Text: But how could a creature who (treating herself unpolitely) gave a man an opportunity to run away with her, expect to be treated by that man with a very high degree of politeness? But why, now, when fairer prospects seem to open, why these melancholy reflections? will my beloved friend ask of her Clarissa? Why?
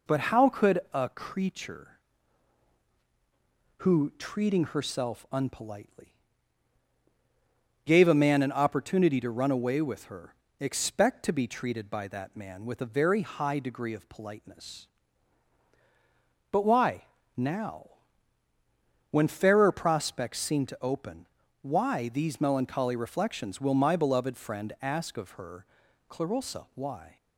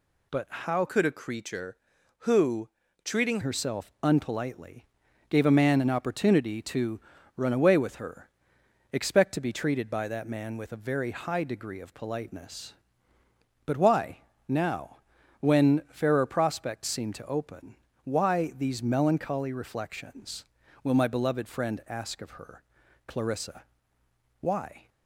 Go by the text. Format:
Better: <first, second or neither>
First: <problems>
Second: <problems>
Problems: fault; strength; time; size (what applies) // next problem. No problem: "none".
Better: first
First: pauses between "her" and "Clarissa"; at 25.6 s; 0.44 s long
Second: changes voice from "could" to "treating"; from 0.8 to 3.3 s; 2.5 s long // pauses between "to" and "run"; slight; at 7.0 s; 0.34 s long // pauses between "her" and "Clarissa"; noticeable; at 22.6 s; 0.46 s long